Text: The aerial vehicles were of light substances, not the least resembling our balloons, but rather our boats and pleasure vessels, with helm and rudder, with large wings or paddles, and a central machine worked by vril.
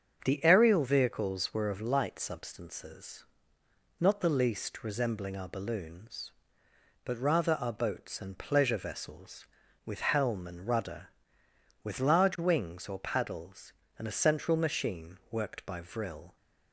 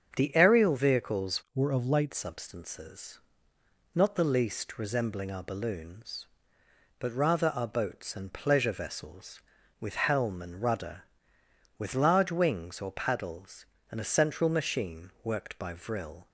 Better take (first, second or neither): first